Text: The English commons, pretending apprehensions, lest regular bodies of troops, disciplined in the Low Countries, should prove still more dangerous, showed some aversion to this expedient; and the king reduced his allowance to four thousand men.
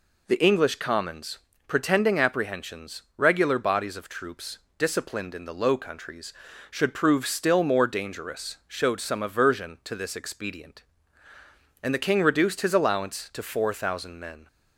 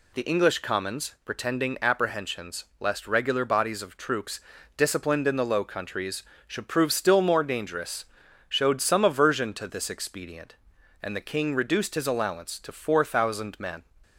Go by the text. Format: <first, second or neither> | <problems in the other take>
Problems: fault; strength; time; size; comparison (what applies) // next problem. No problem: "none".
second | skips "lest"; at 3.0 s